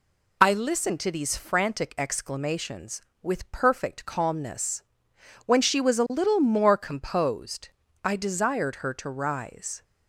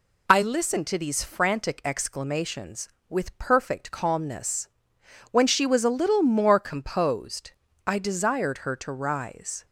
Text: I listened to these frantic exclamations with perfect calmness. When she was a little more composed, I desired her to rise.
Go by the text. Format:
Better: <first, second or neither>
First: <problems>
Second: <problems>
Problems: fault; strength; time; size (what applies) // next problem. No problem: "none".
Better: neither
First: none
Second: none